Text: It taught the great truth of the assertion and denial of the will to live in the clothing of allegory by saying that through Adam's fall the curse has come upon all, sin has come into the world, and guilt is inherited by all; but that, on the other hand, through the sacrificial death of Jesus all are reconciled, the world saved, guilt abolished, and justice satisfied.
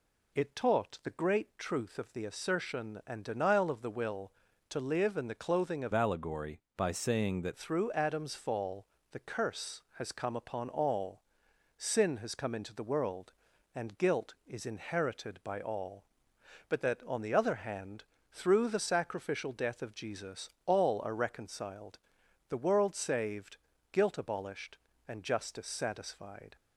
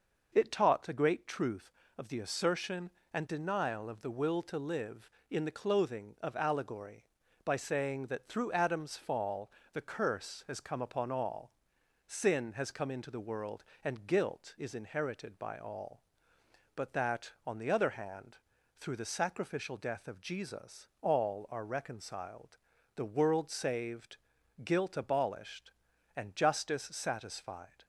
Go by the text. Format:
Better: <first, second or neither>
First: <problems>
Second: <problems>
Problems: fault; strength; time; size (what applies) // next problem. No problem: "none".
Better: second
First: changes voice from "allegory" to "that"; from 5.9 to 7.5 s; 1.6 s long // pauses between "fall" and "the"; slight; at 8.8 s; 0.26 s long // pauses between "Jesus" and "all"; slight; at 20.4 s; 0.16 s long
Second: pauses between "fall" and "the"; slight; at 9.5 s; 0.24 s long